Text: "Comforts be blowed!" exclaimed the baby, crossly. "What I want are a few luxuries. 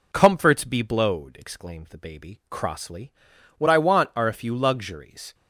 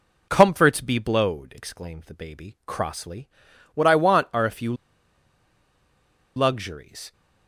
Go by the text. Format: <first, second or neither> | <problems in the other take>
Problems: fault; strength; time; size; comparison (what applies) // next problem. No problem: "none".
first | pauses between "few" and "luxuries"; strong; at 4.7 s; 1.6 s long